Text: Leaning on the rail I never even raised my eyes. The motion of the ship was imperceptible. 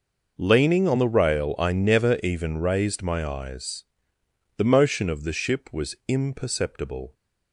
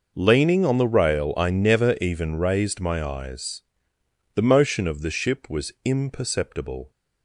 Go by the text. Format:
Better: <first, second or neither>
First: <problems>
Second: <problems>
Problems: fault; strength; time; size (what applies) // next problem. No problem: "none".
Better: neither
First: none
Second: none